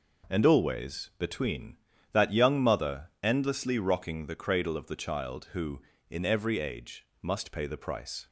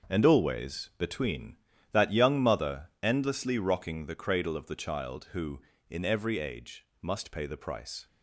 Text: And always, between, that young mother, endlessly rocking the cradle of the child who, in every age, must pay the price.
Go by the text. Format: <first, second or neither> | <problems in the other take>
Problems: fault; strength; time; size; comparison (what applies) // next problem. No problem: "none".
first | gets quieter; strong; throughout; 10 dB